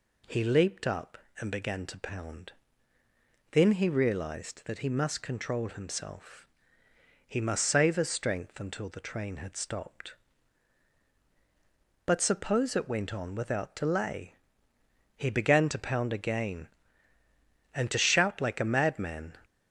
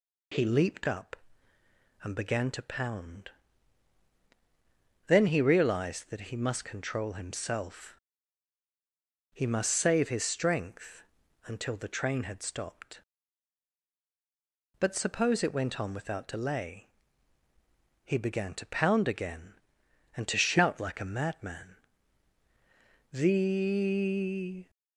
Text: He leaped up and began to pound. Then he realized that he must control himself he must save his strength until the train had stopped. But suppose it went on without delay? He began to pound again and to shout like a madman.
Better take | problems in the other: first | pauses between "himself" and "he"; strong; at 7.9 s; 1.3 s long; noticeable in the first // pauses between "strength" and "until"; at 11.0 s; 0.42 s long // goes on to say "The"; from 23.1 s on; 1.5 s long

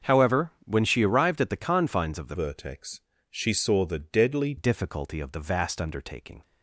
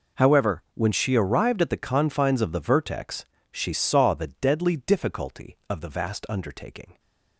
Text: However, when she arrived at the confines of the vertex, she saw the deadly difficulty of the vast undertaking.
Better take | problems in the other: second | starts louder than the rest; until 1.1 s; 6.5 dB // changes voice from "vertex" to "deadly"; from 2.3 to 4.5 s; 2.2 s long

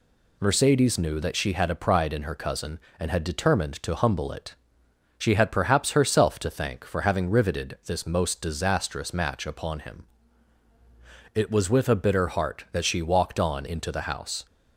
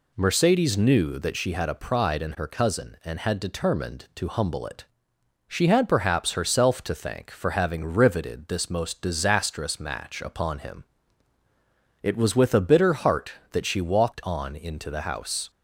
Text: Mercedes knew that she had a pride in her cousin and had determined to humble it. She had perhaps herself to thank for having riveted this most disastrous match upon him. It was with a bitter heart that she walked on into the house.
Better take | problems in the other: neither | none

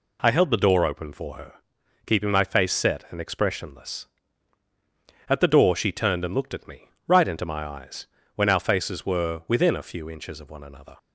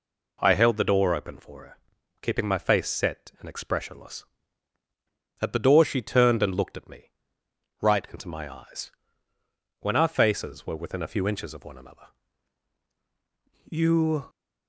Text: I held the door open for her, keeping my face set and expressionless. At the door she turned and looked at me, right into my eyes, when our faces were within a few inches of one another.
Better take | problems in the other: first | goes on to say "You"; from 13.6 s on; 0.60 s long

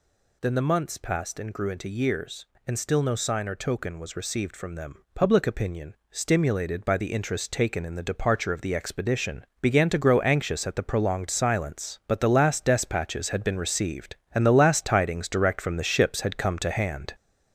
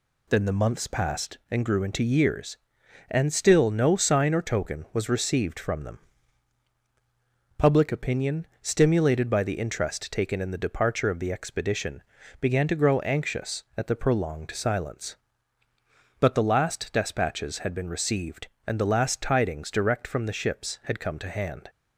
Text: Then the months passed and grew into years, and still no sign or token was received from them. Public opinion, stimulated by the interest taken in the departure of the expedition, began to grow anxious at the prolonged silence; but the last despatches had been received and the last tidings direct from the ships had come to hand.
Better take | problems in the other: second | gets louder; noticeable; throughout; 5 dB

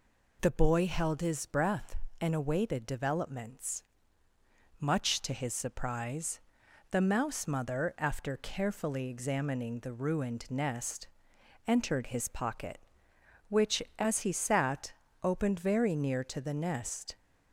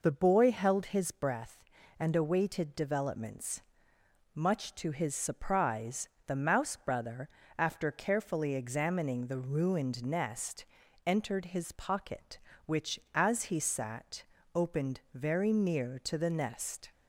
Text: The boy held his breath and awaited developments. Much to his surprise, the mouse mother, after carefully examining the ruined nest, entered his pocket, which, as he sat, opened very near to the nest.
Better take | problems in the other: first | says "brother" for "mother"; at 6.7 s

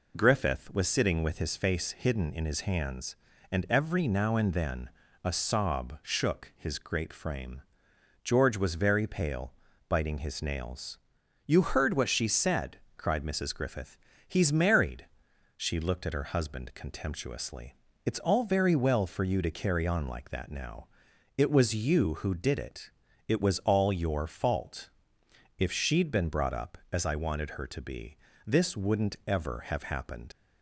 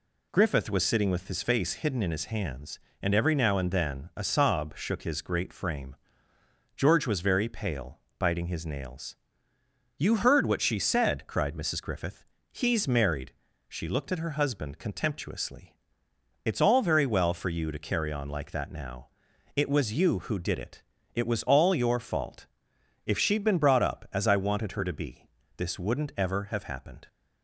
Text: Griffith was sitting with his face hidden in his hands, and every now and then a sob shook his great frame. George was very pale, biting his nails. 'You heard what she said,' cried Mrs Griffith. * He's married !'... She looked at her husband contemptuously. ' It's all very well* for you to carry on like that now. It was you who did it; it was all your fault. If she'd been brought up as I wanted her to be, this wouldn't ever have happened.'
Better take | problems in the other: second | pauses between "then" and "a"; slight; at 4.8 s; 0.34 s long // leaves "happened" unfinished; at 30.3 s; 75 ms

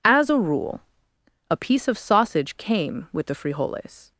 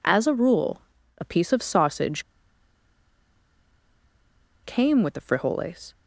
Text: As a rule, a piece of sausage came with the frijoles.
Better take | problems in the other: first | pauses between "sausage" and "came"; strong; at 2.2 s; 2.4 s long

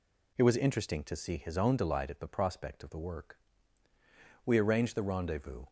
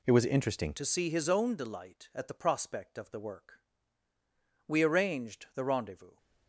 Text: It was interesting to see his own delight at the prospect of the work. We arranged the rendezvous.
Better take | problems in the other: first | changes voice at "to"; from 0.7 s on; 5.4 s long

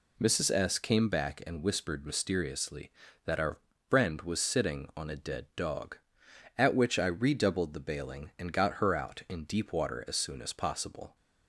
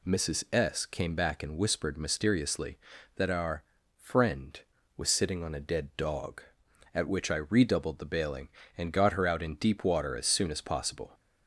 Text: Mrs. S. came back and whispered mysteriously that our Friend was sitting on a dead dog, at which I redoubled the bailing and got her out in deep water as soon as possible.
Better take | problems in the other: neither | pauses between "our" and "Friend"; the same in both

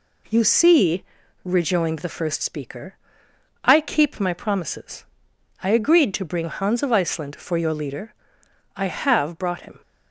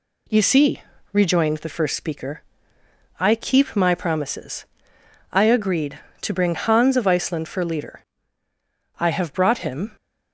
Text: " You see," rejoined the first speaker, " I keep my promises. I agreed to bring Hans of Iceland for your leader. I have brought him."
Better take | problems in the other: first | skips "your"; at 7.6 s

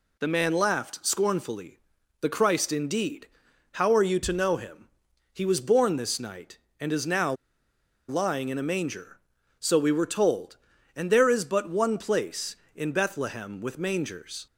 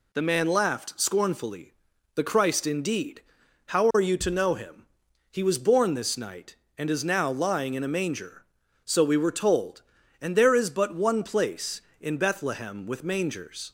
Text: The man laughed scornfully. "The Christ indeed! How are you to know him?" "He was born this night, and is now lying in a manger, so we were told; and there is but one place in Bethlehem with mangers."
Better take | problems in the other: second | pauses between "now" and "lying"; noticeable; at 7.3 s; 0.74 s long

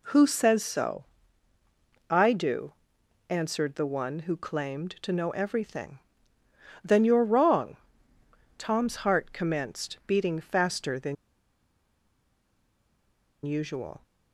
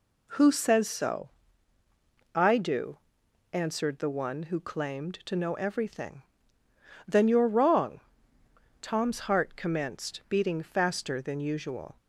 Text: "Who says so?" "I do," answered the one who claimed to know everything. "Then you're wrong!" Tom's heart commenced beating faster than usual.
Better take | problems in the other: second | pauses between "than" and "usual"; strong; at 11.1 s; 2.3 s long

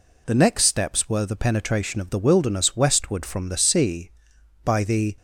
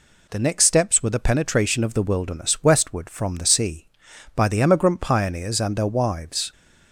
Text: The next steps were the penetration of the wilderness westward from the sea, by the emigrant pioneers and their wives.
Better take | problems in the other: second | stops before "emigrant pioneers and their wives"; at 5.1 s

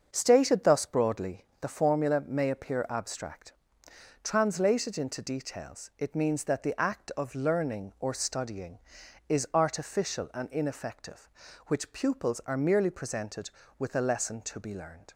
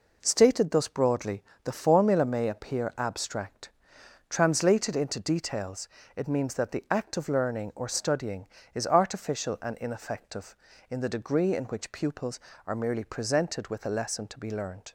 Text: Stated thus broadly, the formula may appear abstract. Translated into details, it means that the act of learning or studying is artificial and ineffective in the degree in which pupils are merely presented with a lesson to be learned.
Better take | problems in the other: second | starts louder than the rest; until 1.1 s; 6.5 dB // skips "in the degree in"; at 11.4 s

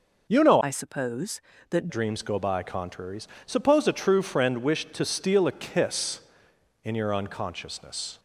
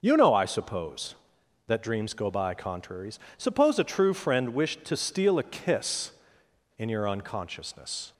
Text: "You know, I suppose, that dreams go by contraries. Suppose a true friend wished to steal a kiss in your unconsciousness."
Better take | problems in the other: second | changes voice from "I" to "that"; from 0.6 to 1.8 s; 1.2 s long

